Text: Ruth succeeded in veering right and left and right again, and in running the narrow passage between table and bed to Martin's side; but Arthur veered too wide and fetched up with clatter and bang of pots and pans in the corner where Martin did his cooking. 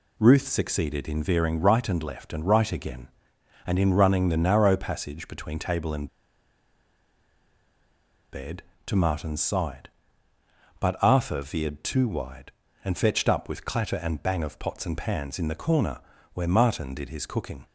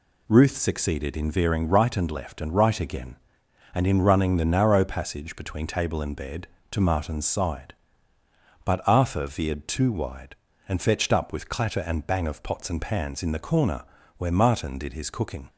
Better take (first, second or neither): second